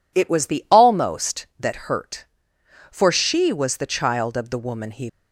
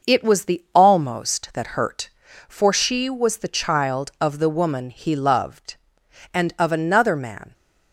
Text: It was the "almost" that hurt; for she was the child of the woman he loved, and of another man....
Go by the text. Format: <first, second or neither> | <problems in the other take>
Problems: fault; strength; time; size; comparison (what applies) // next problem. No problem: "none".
second | stops before "loved and of another man"; at 5.0 s